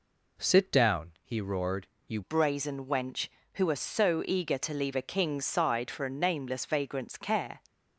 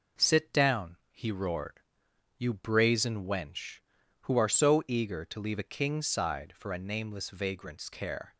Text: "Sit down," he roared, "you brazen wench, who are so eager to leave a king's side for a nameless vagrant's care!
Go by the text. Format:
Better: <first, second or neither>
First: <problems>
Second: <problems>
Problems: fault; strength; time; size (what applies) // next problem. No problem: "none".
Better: second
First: changes voice at "brazen"; from 2.2 s on; 5.4 s long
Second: none